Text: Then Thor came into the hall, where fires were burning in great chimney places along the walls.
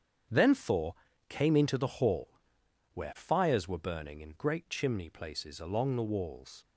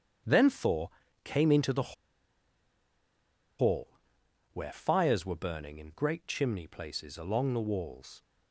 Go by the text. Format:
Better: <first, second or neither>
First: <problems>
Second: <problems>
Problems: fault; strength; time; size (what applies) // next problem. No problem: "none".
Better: first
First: starts louder than the rest; strong; until 1.6 s; 8 dB // pauses between "Thor" and "came"; slight; at 0.9 s; 0.34 s long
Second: starts louder than the rest; strong; until 1.6 s; 8 dB // pauses between "Thor" and "came"; slight; at 0.8 s; 0.34 s long // pauses between "the" and "hall"; strong; at 1.9 s; 1.6 s long